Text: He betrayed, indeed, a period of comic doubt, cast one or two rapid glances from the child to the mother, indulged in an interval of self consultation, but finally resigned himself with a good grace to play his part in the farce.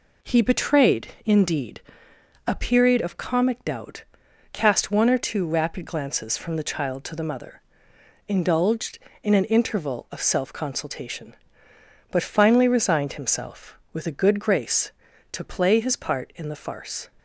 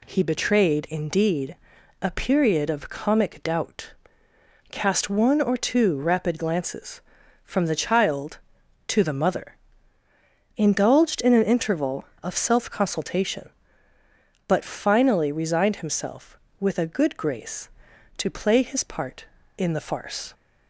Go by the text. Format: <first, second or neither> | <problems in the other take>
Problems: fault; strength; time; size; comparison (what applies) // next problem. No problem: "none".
neither | none